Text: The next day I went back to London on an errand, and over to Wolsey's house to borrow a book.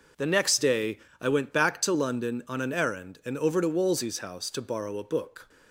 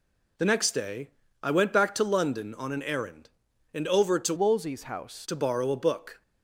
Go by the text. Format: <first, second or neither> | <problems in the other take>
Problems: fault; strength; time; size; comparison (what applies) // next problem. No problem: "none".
first | pauses between "day" and "I"; slight; at 1.0 s; 0.34 s long; slight in the first // changes voice from "Wolsey's" to "house"; from 4.3 to 5.2 s; 0.9 s long